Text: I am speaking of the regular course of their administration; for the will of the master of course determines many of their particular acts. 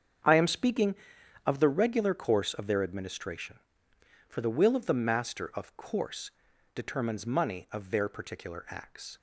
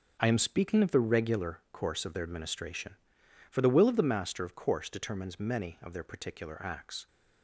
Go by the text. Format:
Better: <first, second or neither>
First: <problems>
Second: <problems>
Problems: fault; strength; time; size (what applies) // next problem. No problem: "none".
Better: second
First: starts louder than the rest; strong; until 1.7 s; 7.5 dB // pauses between "course" and "determines"; at 6.3 s; 0.42 s long // says "money" for "many"; at 7.2 s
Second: starts louder than the rest; until 1.2 s; 7 dB